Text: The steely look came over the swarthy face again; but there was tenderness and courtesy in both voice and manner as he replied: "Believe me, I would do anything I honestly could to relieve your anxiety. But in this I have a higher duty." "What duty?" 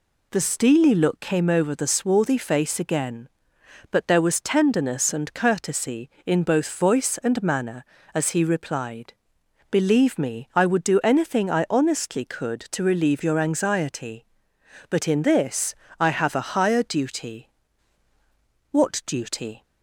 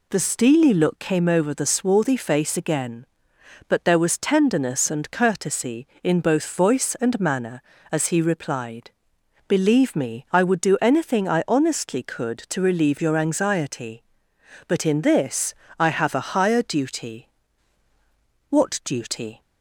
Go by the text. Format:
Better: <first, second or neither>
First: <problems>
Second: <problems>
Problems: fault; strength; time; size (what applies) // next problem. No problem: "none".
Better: neither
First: pauses between "this" and "I"; slight; at 15.7 s; 0.24 s long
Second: pauses between "this" and "I"; slight; at 15.5 s; 0.24 s long